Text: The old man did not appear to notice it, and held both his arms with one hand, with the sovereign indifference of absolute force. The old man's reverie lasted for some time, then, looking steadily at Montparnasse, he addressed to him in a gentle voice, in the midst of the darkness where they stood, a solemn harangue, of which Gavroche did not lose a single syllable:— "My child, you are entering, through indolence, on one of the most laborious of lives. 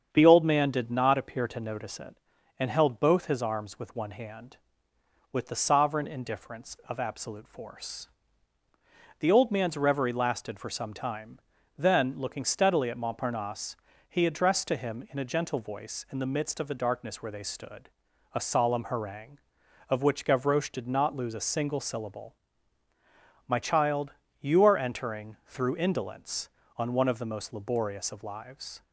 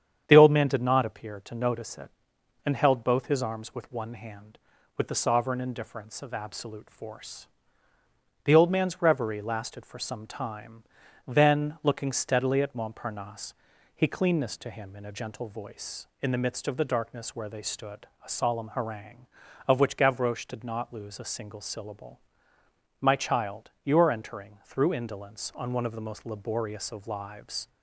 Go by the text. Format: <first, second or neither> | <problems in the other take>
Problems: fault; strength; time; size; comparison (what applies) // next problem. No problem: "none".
first | starts louder than the rest; strong; until 1.2 s; 8.5 dB; strong in the first // says "cleanness" for "addressed"; at 14.0 s